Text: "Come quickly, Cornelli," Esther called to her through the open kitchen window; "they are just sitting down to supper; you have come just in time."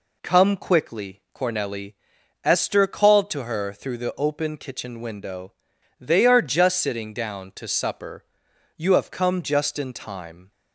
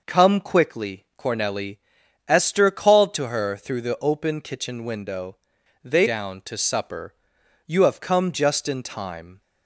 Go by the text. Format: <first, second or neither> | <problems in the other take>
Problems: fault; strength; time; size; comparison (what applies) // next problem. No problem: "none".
first | skips "are just sitting"; at 6.0 s